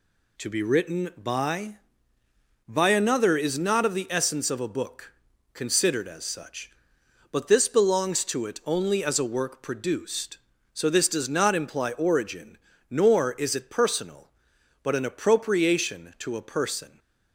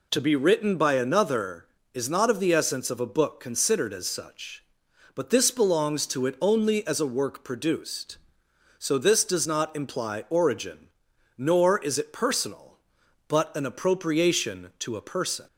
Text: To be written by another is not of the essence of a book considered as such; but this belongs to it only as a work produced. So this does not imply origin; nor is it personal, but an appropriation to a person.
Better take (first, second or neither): second